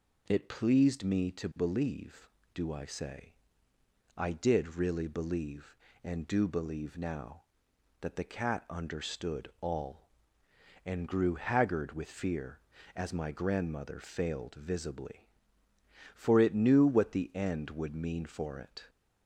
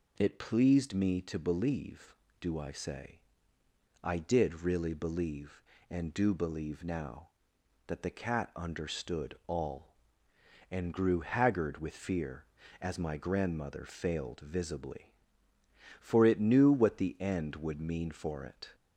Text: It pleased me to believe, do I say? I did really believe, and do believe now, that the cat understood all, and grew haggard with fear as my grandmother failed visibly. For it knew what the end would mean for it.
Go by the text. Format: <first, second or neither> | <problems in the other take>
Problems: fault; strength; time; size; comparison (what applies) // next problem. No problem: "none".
neither | none